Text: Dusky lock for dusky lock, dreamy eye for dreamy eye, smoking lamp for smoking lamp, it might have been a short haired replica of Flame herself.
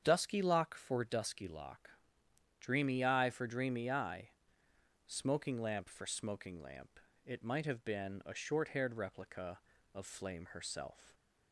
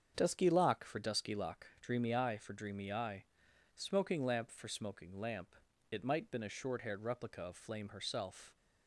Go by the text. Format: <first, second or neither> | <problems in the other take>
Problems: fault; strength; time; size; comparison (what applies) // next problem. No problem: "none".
first | starts louder than the rest; strong; until 1.1 s; 7 dB; strong in the first // skips "have"; at 6.2 s